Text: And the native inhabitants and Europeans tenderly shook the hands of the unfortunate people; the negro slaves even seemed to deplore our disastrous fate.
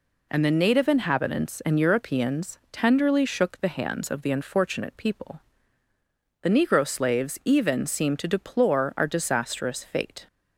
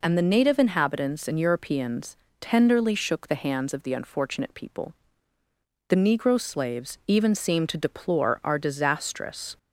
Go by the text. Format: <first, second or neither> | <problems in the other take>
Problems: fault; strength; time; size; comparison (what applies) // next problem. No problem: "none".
first | pauses between "Europeans" and "tenderly"; slight; at 2.1 s; 0.24 s long // stops before "fate"; at 9.5 s